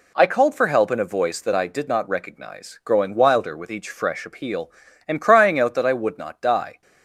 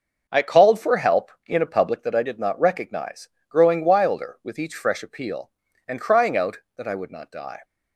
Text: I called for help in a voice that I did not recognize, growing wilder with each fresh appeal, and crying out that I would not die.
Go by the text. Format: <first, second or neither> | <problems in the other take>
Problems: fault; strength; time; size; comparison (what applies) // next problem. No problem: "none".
first | starts louder than the rest; until 1.2 s; 6 dB // says "public" for "voice"; at 1.6 s